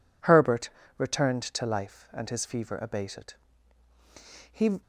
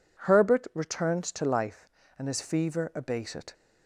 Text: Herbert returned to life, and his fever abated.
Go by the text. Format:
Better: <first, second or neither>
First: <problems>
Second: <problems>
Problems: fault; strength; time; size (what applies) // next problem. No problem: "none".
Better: second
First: pauses between "Herbert" and "returned"; slight; at 0.6 s; 0.28 s long // goes on to say "He"; slight; from 4.5 s on; 0.30 s long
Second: none